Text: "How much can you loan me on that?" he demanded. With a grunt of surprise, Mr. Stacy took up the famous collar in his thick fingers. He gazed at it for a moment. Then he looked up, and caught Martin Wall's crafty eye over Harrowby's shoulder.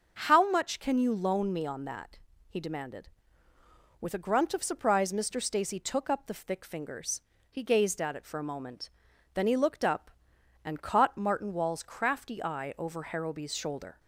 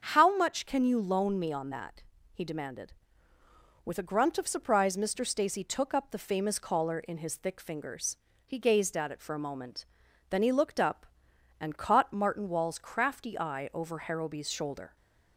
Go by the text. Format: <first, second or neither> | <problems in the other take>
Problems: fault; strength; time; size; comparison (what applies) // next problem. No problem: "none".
second | starts louder than the rest; until 1.2 s; 6.5 dB; strong in the second // skips "famous collar in his"; at 6.4 s